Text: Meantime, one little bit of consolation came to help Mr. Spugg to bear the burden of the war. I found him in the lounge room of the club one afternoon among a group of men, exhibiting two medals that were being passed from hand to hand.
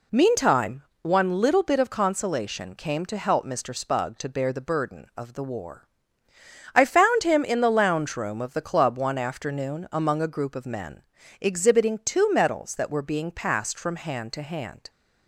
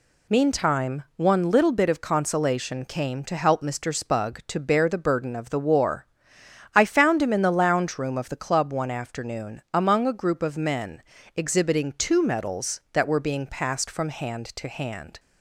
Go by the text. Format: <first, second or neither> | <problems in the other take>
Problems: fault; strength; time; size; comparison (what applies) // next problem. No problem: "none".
neither | none